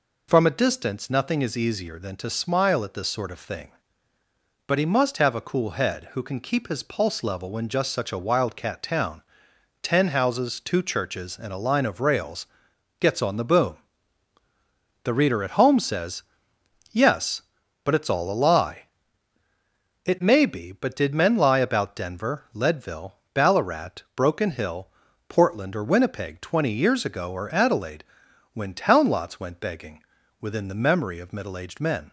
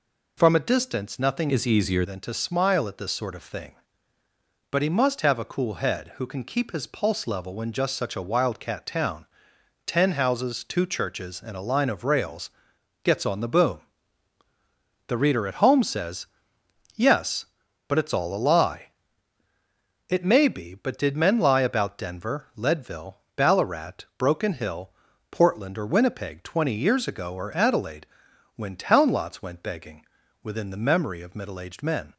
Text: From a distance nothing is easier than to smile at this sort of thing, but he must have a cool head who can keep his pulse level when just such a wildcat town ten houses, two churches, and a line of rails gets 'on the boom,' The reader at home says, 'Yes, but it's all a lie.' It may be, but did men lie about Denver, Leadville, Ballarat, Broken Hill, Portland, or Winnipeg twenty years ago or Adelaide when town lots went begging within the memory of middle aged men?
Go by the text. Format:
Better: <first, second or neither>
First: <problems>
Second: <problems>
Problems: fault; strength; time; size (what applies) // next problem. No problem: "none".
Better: first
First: pauses between "town" and "ten"; noticeable; at 9.2 s; 0.58 s long // pauses between "rails" and "gets"; noticeable; at 12.4 s; 0.54 s long // pauses between "Adelaide" and "when"; noticeable; at 28.0 s; 0.48 s long // pauses between "begging" and "within"; at 30.0 s; 0.42 s long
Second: changes voice from "is" to "easier"; from 1.4 to 2.0 s; 0.6 s long // pauses between "town" and "ten"; noticeable; at 9.2 s; 0.58 s long // pauses between "rails" and "gets"; noticeable; at 12.4 s; 0.54 s long // pauses between "Adelaide" and "when"; noticeable; at 28.0 s; 0.48 s long // pauses between "begging" and "within"; at 30.0 s; 0.42 s long